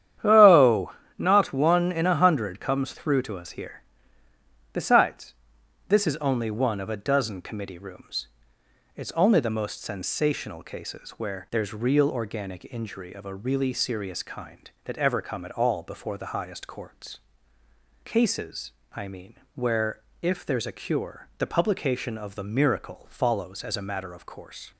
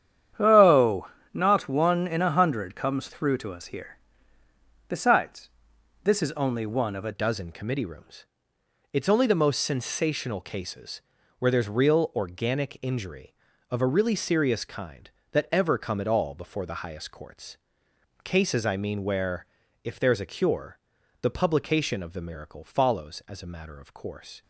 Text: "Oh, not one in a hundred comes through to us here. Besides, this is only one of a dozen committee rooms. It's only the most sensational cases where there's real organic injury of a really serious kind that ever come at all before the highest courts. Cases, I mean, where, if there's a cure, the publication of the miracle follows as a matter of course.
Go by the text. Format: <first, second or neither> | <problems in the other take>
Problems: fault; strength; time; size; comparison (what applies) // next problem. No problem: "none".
first | starts louder than the rest; strong; until 1.6 s; 9.5 dB; strong in the first // changes voice at "dozen"; from 7.1 s on; 17.3 s long // pauses between "cases" and "where"; at 10.9 s; 0.40 s long